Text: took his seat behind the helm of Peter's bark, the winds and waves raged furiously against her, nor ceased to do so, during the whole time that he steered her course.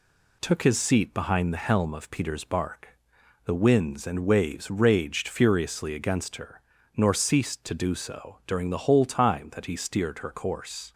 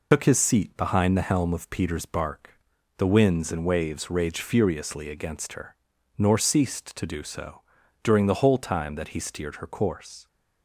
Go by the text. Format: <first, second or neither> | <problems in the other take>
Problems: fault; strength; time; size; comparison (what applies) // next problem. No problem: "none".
first | loses the start of "took"; at 0.1 s; 85 ms